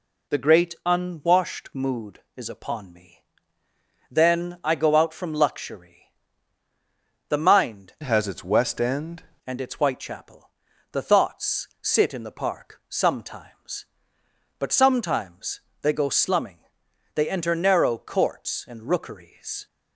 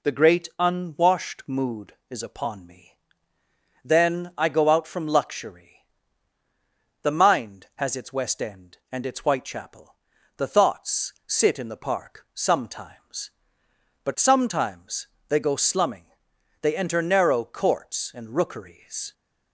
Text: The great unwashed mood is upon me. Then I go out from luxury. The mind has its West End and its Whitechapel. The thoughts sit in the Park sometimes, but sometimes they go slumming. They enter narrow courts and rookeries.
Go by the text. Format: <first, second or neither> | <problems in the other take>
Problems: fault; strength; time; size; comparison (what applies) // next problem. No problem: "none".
second | changes voice from "has" to "End"; from 8.0 to 9.2 s; 1.2 s long // pauses between "thoughts" and "sit"; slight; at 11.6 s; 0.16 s long; slight in the second // pauses between "sometimes" and "they"; slight; at 15.6 s; 0.22 s long; slight in the second